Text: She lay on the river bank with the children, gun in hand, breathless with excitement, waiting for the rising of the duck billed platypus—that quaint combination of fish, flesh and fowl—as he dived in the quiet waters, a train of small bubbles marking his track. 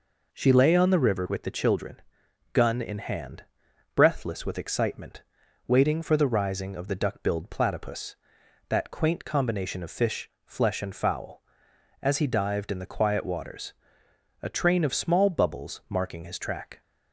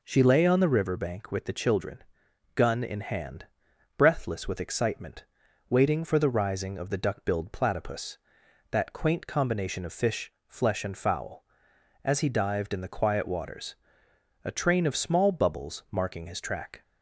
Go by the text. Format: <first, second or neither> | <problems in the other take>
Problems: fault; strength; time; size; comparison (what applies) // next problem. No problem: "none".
second | skips "bank"; at 1.2 s